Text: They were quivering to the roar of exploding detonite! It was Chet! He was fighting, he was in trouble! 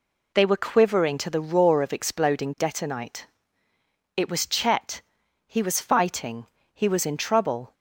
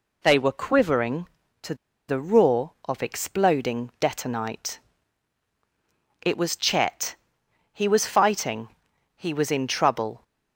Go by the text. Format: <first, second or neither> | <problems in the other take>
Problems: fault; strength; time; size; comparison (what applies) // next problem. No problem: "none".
first | pauses between "to" and "the"; slight; at 1.7 s; 0.34 s long